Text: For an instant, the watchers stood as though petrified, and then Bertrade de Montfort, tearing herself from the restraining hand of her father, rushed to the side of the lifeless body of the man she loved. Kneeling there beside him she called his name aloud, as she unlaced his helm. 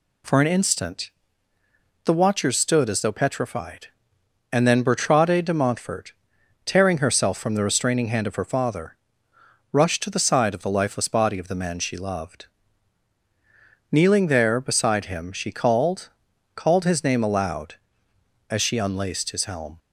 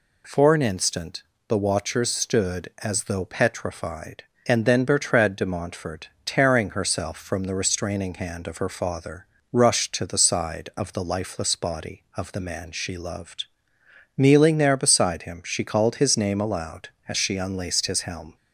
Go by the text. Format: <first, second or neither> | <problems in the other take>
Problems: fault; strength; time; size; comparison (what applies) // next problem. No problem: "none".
second | says "called" twice; at 16.5 s